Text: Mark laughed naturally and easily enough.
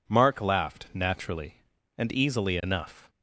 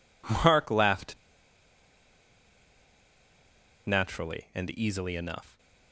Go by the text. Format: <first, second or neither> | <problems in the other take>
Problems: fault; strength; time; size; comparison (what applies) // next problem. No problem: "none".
first | pauses between "laughed" and "naturally"; strong; at 1.1 s; 2.7 s long